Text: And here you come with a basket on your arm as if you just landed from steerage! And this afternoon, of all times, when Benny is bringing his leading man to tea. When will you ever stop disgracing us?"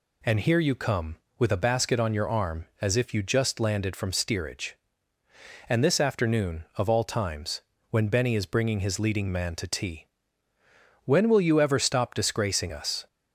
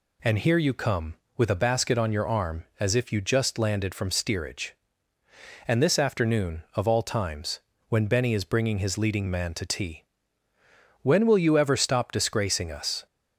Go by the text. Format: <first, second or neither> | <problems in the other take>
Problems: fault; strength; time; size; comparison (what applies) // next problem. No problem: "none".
neither | none